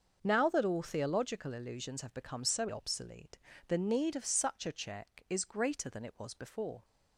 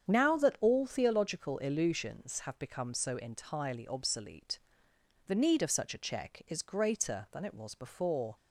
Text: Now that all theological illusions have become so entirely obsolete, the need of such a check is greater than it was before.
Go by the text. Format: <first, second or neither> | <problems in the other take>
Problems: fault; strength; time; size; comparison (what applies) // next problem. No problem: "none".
second | starts louder than the rest; until 1.2 s; 6.5 dB; strong in the second // skips "entirely"; at 2.6 s